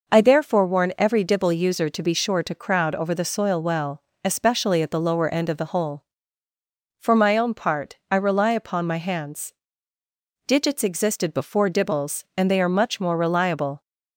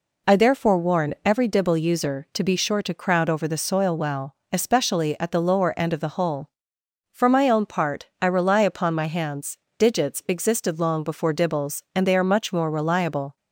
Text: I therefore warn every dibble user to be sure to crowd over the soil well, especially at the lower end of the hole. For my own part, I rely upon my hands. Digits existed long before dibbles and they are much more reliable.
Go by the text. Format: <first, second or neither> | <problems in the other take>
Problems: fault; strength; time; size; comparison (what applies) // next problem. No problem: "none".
second | skips "long"; at 11.3 s